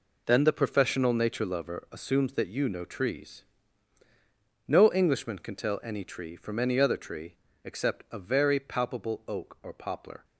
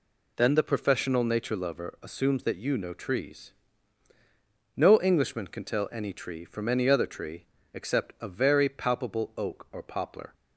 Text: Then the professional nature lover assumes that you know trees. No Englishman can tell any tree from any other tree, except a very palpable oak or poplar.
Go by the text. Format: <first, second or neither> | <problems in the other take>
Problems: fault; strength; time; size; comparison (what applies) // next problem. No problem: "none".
second | gets quieter; strong; throughout; 9.5 dB